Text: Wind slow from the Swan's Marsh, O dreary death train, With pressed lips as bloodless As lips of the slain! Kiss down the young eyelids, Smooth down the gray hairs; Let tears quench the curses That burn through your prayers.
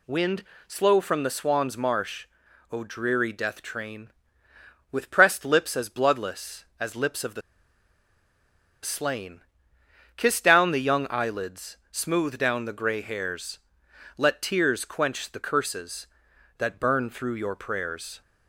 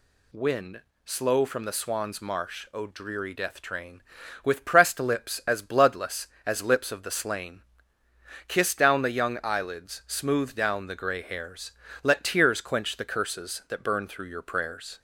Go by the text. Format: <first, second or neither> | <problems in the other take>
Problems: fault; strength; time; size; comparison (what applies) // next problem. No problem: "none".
second | pauses between "Wind" and "slow"; slight; at 0.4 s; 0.24 s long; slight in the second // pauses between "the" and "slain"; strong; at 7.4 s; 1.4 s long